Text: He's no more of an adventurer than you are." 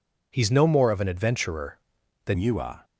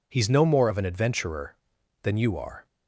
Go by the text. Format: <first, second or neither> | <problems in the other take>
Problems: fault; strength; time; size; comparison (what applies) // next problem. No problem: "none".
second | changes voice at "you"; from 2.3 s on; 0.5 s long